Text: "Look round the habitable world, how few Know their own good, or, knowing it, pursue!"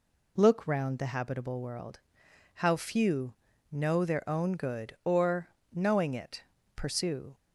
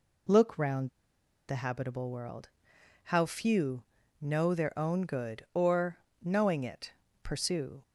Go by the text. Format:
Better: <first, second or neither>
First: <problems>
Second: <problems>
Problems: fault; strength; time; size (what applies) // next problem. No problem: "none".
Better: first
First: pauses between "few" and "Know"; at 3.3 s; 0.38 s long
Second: pauses between "round" and "the"; noticeable; at 0.8 s; 0.58 s long // pauses between "few" and "Know"; at 3.8 s; 0.38 s long